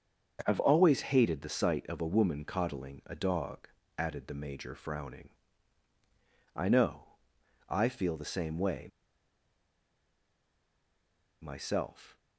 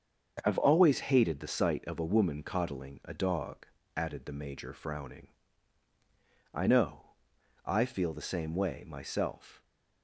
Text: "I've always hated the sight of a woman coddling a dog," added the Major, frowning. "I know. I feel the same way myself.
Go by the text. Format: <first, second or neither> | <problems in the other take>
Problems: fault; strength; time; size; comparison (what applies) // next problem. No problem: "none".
second | starts louder than the rest; until 1.4 s; 7 dB; also in the second // pauses between "way" and "myself"; strong; at 8.8 s; 2.5 s long